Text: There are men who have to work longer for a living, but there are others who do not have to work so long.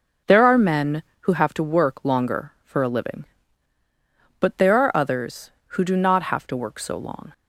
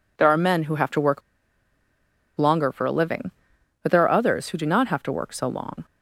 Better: first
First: none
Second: pauses between "work" and "longer"; at 1.2 s; 1.1 s long

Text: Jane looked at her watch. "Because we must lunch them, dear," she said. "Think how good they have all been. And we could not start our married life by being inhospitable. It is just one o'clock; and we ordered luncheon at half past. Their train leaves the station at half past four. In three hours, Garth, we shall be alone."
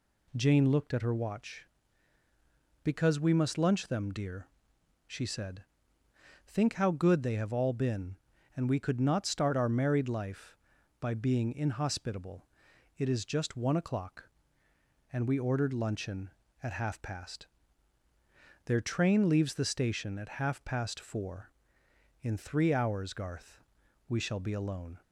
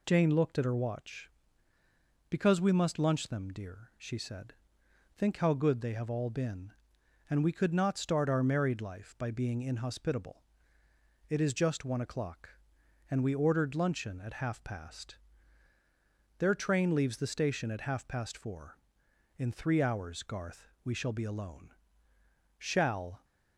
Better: first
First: none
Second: goes on to say "Shall"; noticeable; from 22.5 s on; 0.66 s long

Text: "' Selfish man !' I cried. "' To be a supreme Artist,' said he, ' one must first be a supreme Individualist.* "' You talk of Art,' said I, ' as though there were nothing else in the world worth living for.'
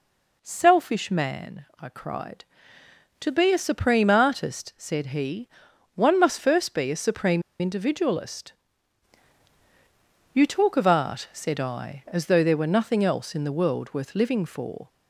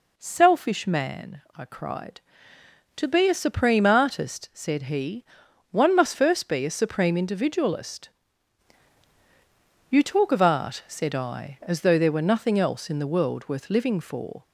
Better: second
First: pauses between "supreme" and "Individualist"; slight; at 7.4 s; 0.18 s long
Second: none

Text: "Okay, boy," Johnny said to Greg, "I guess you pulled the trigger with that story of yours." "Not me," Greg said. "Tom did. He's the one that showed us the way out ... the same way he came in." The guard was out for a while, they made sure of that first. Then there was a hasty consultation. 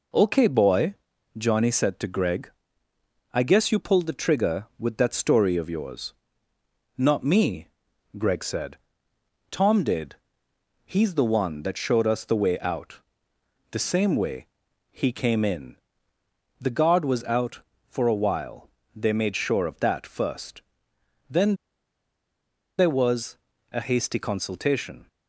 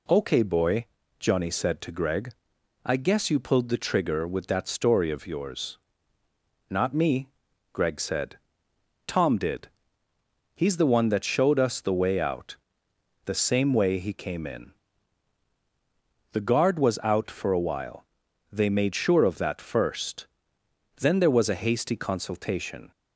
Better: second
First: pauses between "way" and "he"; at 14.4 s; 0.42 s long // pauses between "Then" and "there"; at 21.5 s; 1.2 s long // pauses between "was" and "a"; slight; at 23.3 s; 0.34 s long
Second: none

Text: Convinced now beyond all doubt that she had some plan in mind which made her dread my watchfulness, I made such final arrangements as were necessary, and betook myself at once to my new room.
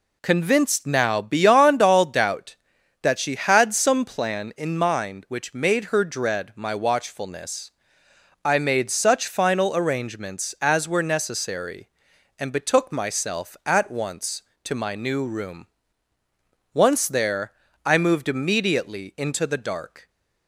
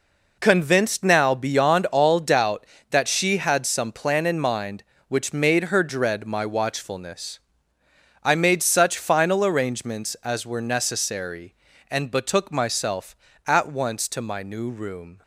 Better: second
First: goes on to say "Once there I moved immediately into the dark"; strong; from 16.7 s on; 3.3 s long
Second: none

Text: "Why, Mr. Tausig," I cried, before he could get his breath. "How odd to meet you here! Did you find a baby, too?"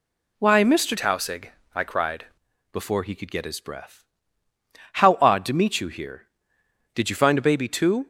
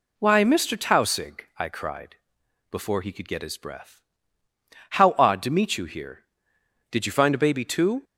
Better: second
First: changes voice from "Tausig" to "cried"; from 0.9 to 2.2 s; 1.3 s long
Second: none

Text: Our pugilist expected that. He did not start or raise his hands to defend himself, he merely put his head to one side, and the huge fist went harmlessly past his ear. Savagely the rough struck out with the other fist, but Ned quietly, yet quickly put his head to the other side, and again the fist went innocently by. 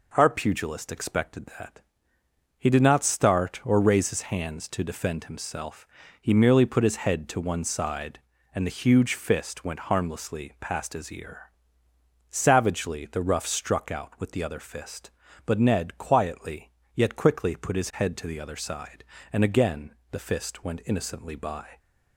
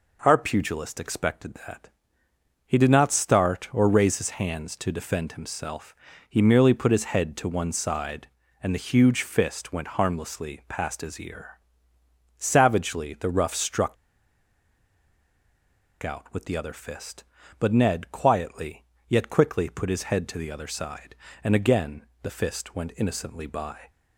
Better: first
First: pauses between "again" and "the"; slight; at 19.9 s; 0.18 s long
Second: pauses between "struck" and "out"; strong; at 13.9 s; 2.0 s long // pauses between "again" and "the"; slight; at 22.0 s; 0.18 s long

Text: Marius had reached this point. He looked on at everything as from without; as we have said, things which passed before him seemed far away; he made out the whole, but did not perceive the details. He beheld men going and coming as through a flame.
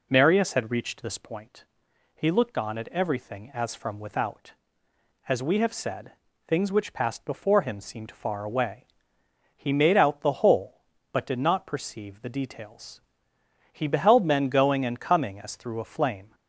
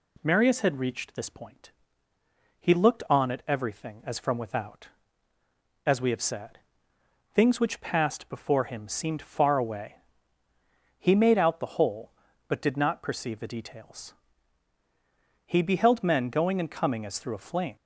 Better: neither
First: none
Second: none

